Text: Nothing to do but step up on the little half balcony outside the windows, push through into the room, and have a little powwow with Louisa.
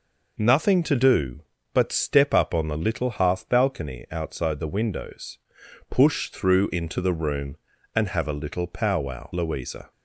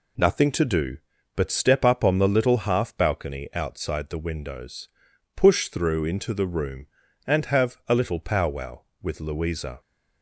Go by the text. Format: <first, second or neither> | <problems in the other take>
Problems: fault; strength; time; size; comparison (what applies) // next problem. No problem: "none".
second | skips "with"; at 9.3 s